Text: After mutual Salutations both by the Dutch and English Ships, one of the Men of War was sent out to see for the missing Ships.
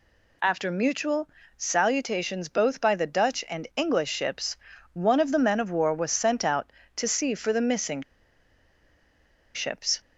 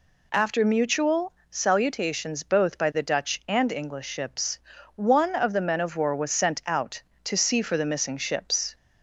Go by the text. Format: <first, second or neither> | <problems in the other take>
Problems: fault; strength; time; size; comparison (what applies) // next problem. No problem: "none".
second | pauses between "mutual" and "Salutations"; slight; at 1.2 s; 0.28 s long; slight in the second // pauses between "missing" and "Ships"; strong; at 8.0 s; 1.5 s long